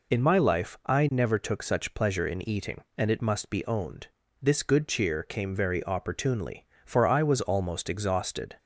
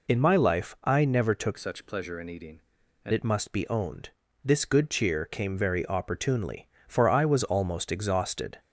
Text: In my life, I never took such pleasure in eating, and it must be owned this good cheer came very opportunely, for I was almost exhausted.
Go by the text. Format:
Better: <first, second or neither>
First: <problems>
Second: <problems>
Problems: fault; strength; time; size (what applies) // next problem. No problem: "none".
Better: first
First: pauses between "owned" and "this"; slight; at 4.0 s; 0.34 s long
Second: changes voice from "such" to "and"; from 1.5 to 3.1 s; 1.6 s long // pauses between "owned" and "this"; slight; at 4.1 s; 0.34 s long